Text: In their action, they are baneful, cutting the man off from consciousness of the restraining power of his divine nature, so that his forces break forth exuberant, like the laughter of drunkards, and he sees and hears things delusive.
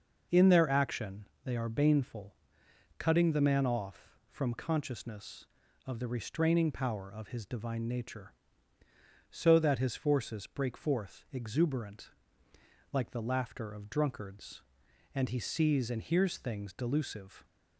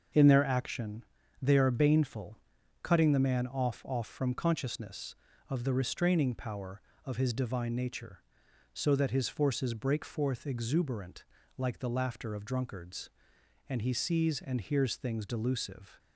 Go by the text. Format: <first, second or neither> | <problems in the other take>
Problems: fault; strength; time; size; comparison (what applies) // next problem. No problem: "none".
first | starts louder than the rest; until 1.5 s; 6.5 dB // says "off" twice; at 3.8 s